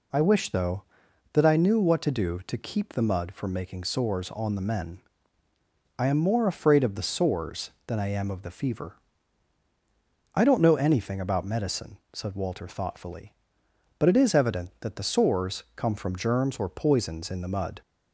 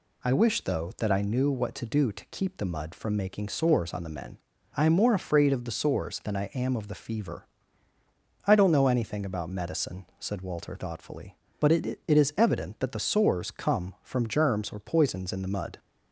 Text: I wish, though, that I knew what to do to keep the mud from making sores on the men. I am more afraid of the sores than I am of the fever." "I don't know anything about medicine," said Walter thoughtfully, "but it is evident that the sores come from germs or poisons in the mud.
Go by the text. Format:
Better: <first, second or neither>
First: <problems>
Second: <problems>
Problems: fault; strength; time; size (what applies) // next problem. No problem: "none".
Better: first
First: none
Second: says "it" twice; at 12.0 s